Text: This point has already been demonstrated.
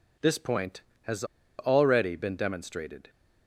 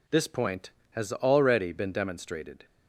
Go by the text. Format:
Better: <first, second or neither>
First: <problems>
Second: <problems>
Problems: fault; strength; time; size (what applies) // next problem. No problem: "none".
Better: second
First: pauses between "has" and "already"; slight; at 1.2 s; 0.35 s long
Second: none